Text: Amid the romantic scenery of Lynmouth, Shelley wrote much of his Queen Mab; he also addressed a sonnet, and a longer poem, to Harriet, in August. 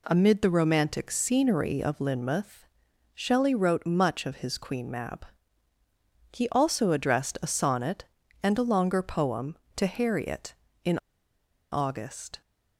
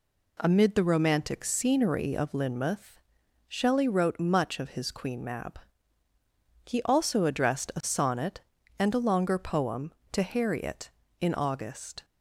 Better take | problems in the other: second | pauses between "in" and "August"; noticeable; at 10.9 s; 0.73 s long

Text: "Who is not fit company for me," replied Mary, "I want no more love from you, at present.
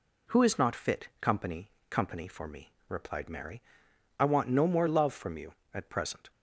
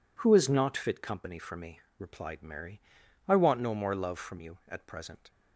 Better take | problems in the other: second | says "company" twice; at 1.8 s

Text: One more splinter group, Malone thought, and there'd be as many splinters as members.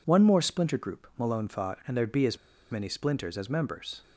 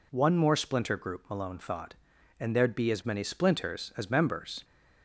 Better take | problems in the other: second | pauses between "as" and "many"; slight; at 2.3 s; 0.33 s long

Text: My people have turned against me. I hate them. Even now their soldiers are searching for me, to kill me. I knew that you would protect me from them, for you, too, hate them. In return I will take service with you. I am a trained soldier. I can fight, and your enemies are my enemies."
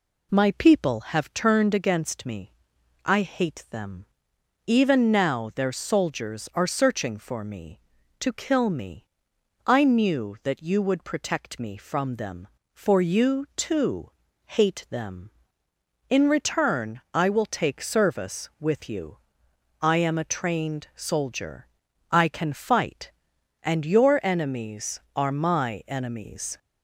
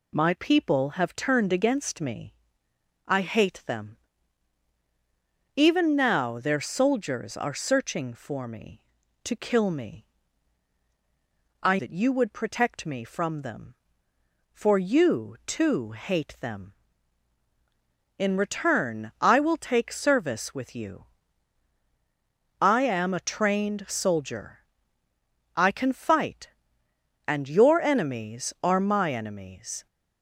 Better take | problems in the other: first | skips "knew"; at 11.7 s

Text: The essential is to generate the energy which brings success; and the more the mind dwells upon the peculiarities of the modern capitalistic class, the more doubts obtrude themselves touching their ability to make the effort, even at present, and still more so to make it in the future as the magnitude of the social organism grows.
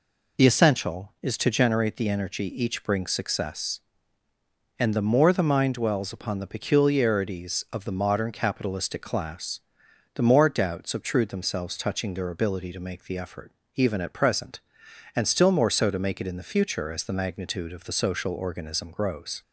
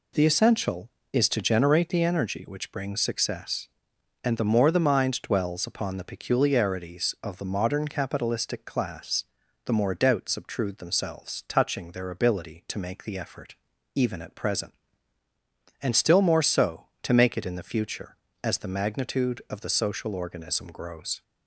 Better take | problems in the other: second | says "each" for "which"; at 2.4 s

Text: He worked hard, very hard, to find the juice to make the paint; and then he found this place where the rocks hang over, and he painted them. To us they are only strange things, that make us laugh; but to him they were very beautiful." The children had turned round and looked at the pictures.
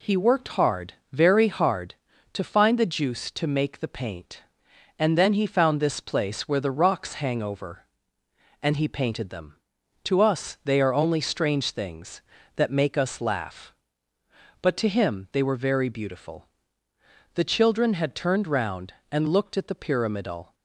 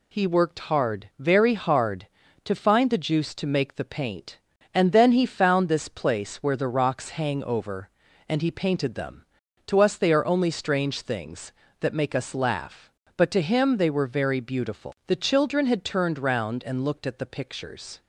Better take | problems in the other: second | says "pyramidal" for "pictures"; at 19.7 s

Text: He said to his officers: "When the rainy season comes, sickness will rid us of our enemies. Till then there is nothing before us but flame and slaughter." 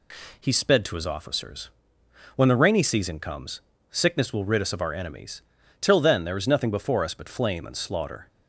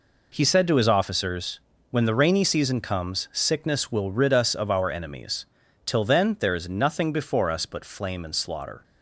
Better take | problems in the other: second | says "sped" for "said"; at 0.5 s

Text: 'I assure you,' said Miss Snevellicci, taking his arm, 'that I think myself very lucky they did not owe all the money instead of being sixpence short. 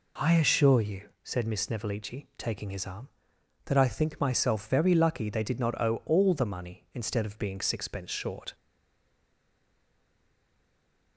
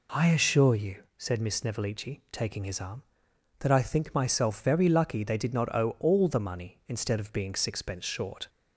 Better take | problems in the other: second | stays silent after the last word; strong; from 8.5 s on; 2.6 s long

